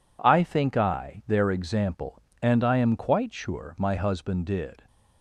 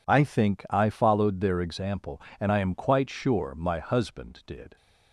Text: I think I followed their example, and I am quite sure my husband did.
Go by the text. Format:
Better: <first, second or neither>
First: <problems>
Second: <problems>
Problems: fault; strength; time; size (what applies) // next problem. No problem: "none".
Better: second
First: skips "followed"; at 1.2 s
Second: none